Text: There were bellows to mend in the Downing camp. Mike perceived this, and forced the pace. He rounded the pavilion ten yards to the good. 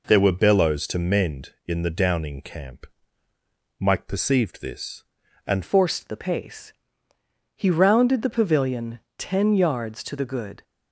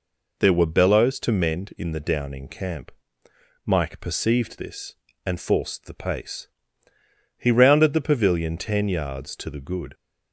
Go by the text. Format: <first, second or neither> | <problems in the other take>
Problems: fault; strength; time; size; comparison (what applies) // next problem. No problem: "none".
second | changes voice at "forced"; from 5.6 s on; 5.0 s long // pauses between "pavilion" and "ten"; slight; at 8.9 s; 0.18 s long